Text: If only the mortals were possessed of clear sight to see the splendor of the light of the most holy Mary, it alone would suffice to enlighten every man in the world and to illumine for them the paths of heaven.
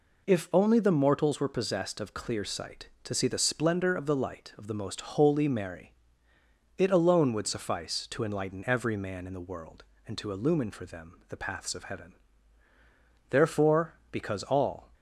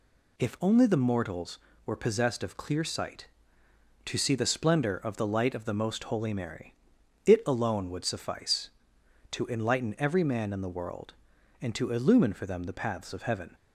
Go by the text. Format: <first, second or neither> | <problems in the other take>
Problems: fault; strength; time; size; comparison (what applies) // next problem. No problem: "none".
second | goes on to say "Therefore because all"; from 13.2 s on; 1.6 s long